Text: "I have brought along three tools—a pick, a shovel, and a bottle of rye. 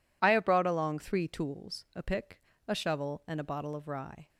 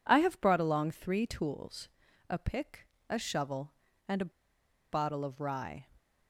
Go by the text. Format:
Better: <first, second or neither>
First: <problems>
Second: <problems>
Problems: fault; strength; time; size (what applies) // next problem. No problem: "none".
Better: first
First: none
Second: pauses between "a" and "bottle"; noticeable; at 4.3 s; 0.61 s long